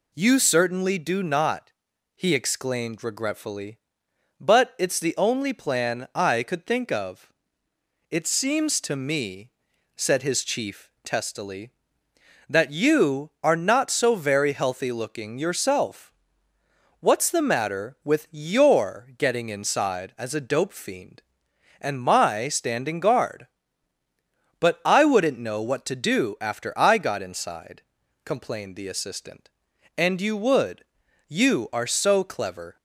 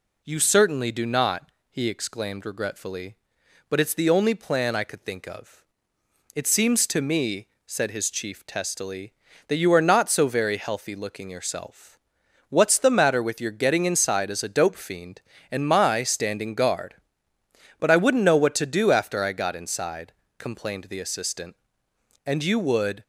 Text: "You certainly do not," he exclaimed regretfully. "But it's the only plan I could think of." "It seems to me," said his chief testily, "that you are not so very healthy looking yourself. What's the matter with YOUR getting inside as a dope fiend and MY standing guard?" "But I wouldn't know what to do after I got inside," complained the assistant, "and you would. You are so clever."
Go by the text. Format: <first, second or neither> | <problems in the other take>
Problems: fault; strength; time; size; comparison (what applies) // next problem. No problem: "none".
first | stops before "You are so clever"; at 23.0 s